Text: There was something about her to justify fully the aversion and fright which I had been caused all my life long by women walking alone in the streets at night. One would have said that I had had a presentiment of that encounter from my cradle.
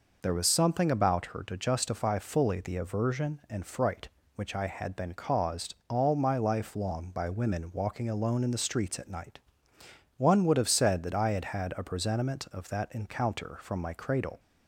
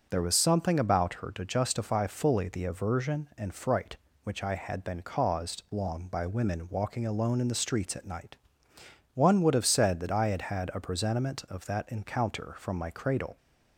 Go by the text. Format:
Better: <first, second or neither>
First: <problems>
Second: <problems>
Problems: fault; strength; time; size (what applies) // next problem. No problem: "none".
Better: first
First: none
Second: skips "all my life"; at 5.6 s